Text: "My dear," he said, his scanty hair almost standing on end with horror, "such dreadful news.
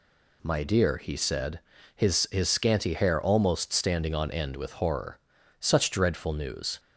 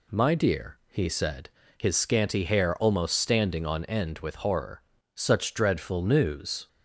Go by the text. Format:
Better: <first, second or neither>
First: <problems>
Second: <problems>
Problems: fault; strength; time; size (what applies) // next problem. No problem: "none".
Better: second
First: says "his" twice; at 2.3 s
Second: none